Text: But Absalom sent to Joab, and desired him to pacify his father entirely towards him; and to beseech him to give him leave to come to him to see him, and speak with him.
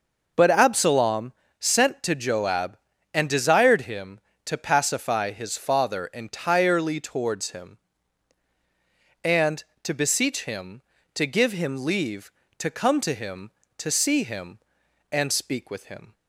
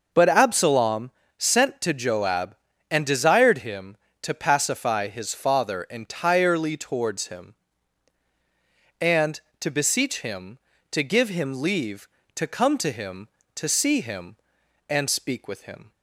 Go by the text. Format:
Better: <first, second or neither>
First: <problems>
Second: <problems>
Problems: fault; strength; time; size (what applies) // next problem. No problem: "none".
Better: neither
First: pauses between "Absalom" and "sent"; slight; at 1.3 s; 0.26 s long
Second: pauses between "Absalom" and "sent"; slight; at 1.1 s; 0.26 s long